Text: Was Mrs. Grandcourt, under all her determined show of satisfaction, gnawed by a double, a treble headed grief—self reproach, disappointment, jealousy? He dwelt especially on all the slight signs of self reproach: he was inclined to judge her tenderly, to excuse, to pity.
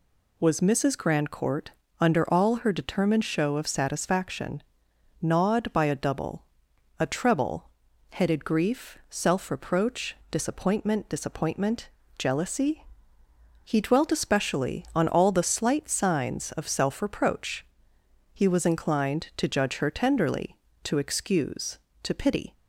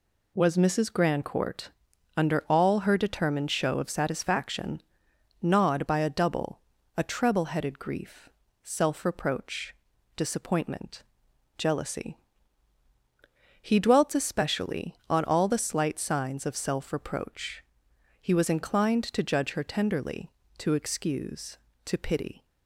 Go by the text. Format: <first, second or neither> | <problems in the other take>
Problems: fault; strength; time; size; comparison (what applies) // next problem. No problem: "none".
second | pauses between "treble" and "headed"; at 7.6 s; 0.42 s long // says "disappointment" twice; at 11.0 s